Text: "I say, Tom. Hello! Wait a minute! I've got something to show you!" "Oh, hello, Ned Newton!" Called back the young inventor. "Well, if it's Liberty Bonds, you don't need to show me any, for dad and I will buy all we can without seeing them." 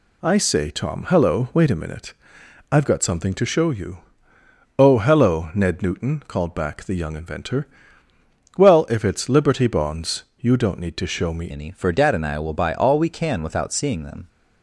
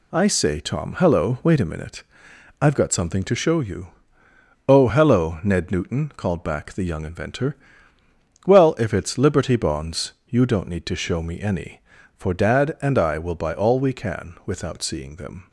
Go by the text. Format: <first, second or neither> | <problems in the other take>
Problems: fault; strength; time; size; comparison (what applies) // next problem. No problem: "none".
second | changes voice at "any"; from 11.5 s on; 2.7 s long